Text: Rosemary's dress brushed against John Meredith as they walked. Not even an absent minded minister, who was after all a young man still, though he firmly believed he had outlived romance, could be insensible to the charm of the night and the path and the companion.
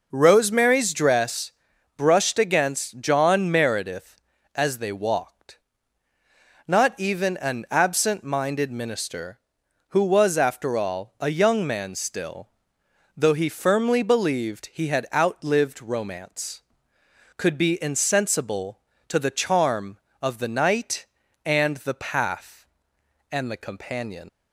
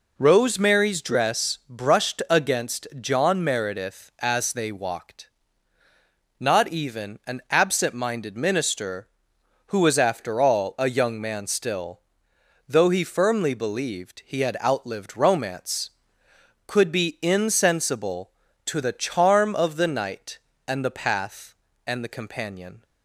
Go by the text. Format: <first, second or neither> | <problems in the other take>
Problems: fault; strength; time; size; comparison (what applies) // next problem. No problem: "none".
second | pauses between "dress" and "brushed"; at 1.5 s; 0.44 s long // leaves "companion" unfinished; at 24.2 s; 95 ms